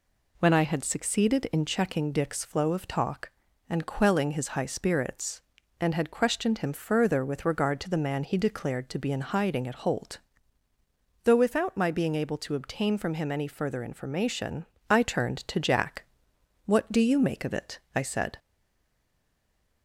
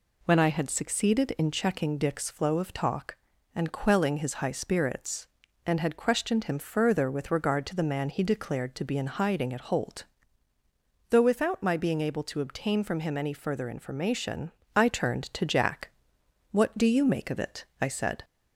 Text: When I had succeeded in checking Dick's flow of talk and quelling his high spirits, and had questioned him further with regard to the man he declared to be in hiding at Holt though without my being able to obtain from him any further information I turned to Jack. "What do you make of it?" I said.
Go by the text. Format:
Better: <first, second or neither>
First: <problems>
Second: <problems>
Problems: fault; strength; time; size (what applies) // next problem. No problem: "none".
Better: second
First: pauses between "Holt" and "though"; at 10.1 s; 1.0 s long // pauses between "information" and "I"; slight; at 14.6 s; 0.24 s long // stays silent after the last word; noticeable; from 18.3 s on; 1.5 s long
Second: pauses between "Holt" and "though"; at 10.0 s; 1.0 s long // pauses between "information" and "I"; slight; at 14.4 s; 0.24 s long